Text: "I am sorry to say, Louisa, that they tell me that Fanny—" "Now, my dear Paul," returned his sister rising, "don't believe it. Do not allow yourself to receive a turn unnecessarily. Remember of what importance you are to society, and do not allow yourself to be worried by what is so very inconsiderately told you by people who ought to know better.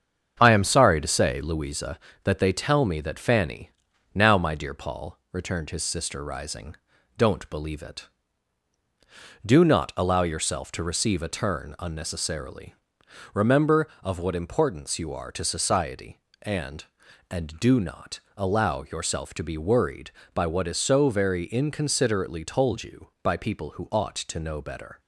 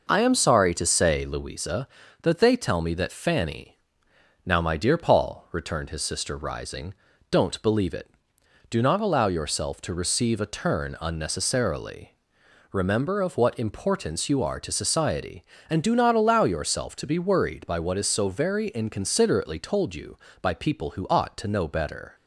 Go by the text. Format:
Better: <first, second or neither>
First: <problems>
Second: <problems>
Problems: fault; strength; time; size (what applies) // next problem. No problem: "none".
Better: second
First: starts louder than the rest; strong; until 1.4 s; 7.5 dB // says "and" twice; at 17.3 s // pauses between "not" and "allow"; slight; at 18.1 s; 0.18 s long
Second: none